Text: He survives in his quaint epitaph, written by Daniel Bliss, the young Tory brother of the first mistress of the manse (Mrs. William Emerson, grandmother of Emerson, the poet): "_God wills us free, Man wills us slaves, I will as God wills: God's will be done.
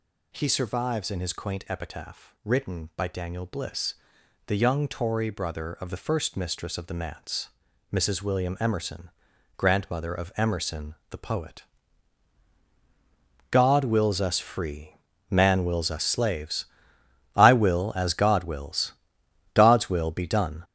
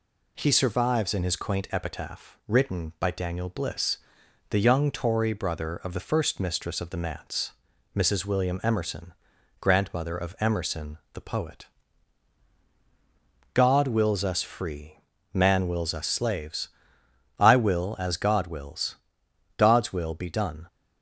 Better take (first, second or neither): second